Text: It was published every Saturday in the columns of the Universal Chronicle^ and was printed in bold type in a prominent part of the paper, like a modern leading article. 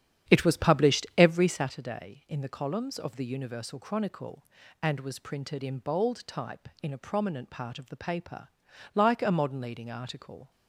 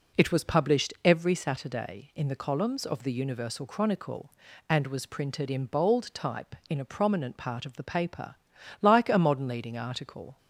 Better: second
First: starts louder than the rest; strong; until 1.7 s; 9.5 dB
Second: none

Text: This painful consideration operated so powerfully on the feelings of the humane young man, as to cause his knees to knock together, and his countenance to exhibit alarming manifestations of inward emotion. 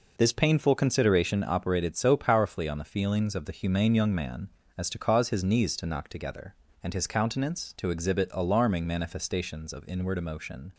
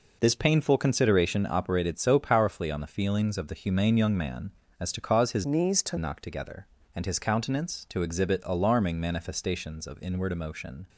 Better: first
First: none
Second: changes voice from "knees" to "to"; from 5.4 to 5.9 s; 0.5 s long

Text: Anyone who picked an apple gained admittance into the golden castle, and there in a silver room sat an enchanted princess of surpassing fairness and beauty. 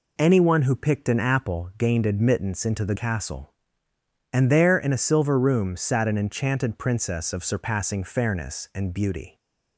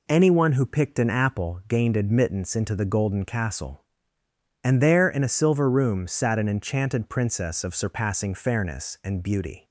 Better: second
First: skips "golden"; at 2.9 s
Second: none

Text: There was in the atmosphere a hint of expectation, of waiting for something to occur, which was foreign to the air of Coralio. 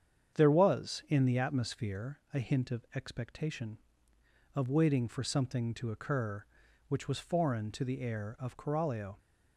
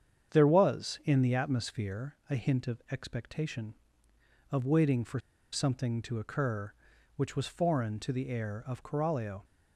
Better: first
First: starts louder than the rest; strong; until 1.4 s; 8 dB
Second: starts louder than the rest; strong; until 1.3 s; 8 dB // pauses between "for" and "something"; slight; at 5.1 s; 0.33 s long

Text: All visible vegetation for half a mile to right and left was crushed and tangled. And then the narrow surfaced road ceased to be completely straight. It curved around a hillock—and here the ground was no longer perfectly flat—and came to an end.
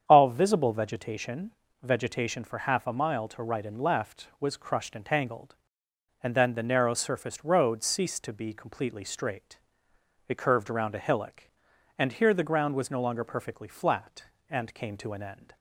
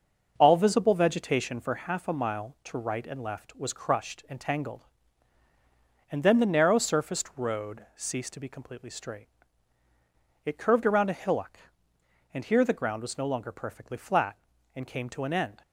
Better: second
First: starts louder than the rest; strong; until 1.0 s; 8 dB // says "vegetation" twice; at 1.8 s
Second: starts louder than the rest; noticeable; until 1.3 s; 6 dB

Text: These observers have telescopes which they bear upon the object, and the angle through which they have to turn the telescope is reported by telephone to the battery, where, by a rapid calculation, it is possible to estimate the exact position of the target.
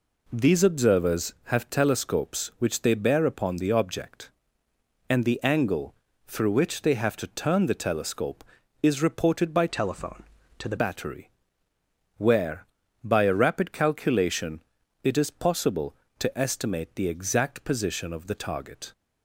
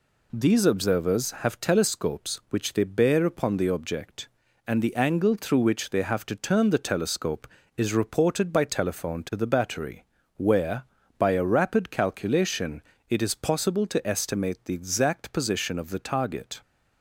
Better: second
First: pauses between "angle" and "through"; slight; at 5.9 s; 0.34 s long // changes voice from "telephone" to "the"; from 9.6 to 10.7 s; 1.1 s long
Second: none

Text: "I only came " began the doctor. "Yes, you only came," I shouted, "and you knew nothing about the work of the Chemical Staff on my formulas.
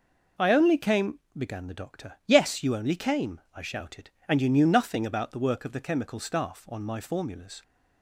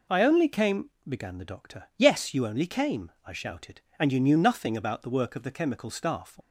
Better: first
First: none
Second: stops before "on my formulas"; at 6.4 s

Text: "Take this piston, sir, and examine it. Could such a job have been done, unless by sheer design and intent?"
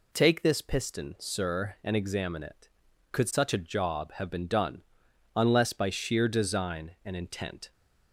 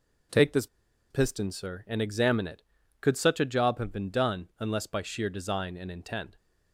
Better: first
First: none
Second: pauses between "this" and "piston"; at 0.6 s; 0.43 s long

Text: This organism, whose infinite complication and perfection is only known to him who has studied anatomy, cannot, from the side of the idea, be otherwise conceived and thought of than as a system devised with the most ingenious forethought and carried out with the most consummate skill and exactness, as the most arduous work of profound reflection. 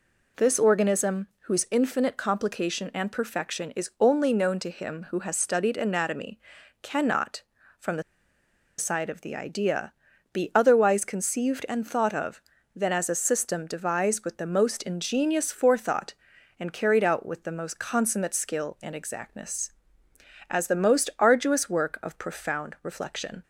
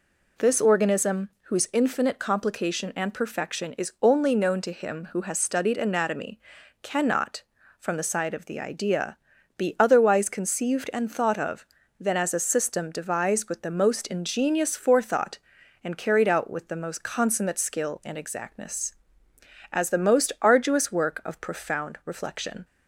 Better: second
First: pauses between "the" and "side"; noticeable; at 8.0 s; 0.75 s long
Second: none

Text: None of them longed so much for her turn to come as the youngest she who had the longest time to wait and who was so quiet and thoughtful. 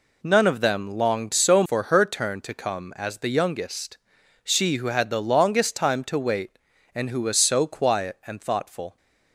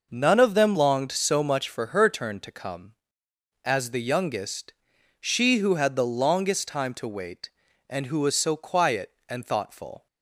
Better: second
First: skips "much"; at 1.6 s // pauses between "youngest" and "she"; noticeable; at 3.9 s; 0.50 s long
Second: pauses between "youngest" and "she"; noticeable; at 4.7 s; 0.46 s long

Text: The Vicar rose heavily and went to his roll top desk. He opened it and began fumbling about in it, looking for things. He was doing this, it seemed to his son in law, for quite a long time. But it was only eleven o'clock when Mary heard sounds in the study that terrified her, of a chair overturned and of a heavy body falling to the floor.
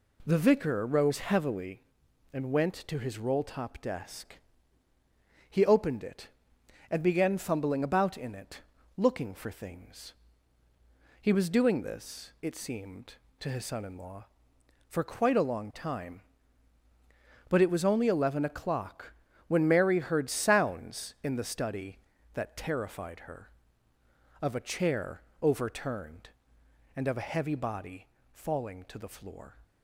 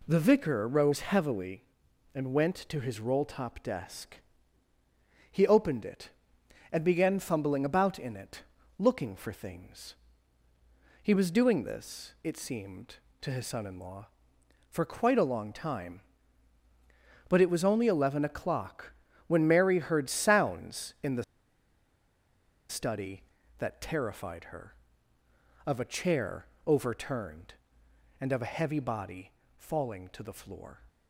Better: first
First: pauses between "o'clock" and "when"; slight; at 19.1 s; 0.36 s long // pauses between "chair" and "overturned"; slight; at 25.2 s; 0.20 s long // pauses between "body" and "falling"; slight; at 28.0 s; 0.26 s long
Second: pauses between "o'clock" and "when"; slight; at 18.9 s; 0.36 s long // pauses between "the" and "study"; strong; at 21.2 s; 1.4 s long // pauses between "chair" and "overturned"; slight; at 26.4 s; 0.20 s long // pauses between "body" and "falling"; slight; at 29.3 s; 0.26 s long

